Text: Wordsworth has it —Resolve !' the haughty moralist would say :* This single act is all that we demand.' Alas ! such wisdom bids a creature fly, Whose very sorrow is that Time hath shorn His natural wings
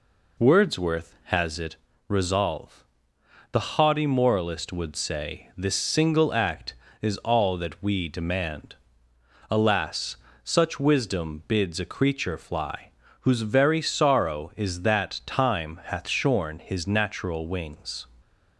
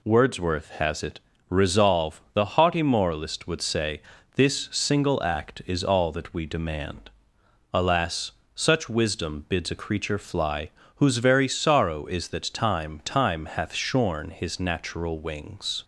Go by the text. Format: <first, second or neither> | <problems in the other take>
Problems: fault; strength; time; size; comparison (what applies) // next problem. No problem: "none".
first | says "Time" twice; at 13.0 s